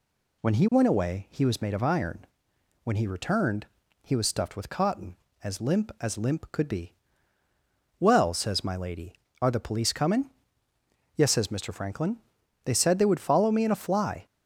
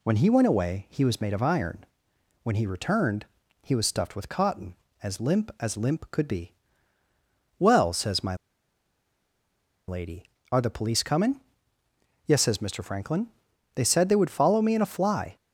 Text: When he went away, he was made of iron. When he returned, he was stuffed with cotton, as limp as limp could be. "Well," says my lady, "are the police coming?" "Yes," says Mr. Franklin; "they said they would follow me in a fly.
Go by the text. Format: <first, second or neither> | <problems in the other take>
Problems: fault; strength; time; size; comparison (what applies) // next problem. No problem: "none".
first | pauses between "my" and "lady"; strong; at 8.3 s; 1.5 s long